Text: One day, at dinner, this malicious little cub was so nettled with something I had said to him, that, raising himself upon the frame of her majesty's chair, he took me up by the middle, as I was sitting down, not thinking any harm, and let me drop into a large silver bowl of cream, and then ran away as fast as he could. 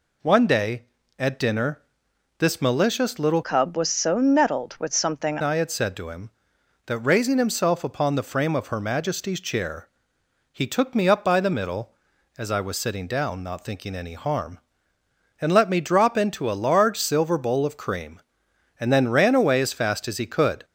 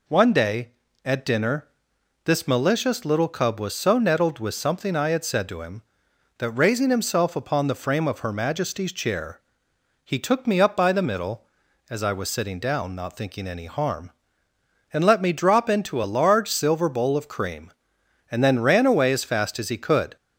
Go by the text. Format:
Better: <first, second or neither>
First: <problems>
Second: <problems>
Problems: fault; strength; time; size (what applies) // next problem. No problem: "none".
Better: second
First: changes voice from "cub" to "something"; from 3.4 to 5.3 s; 1.9 s long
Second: none